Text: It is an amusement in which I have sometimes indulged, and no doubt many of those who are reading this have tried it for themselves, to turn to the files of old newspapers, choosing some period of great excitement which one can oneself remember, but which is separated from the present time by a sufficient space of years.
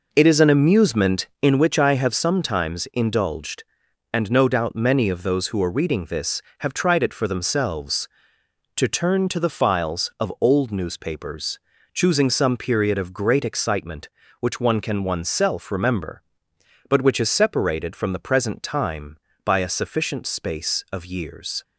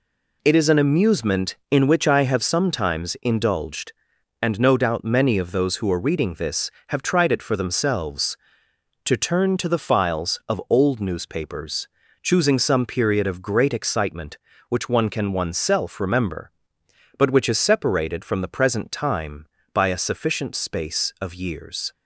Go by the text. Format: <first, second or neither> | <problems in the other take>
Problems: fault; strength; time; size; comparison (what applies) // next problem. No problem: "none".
second | starts louder than the rest; noticeable; until 1.5 s; 5 dB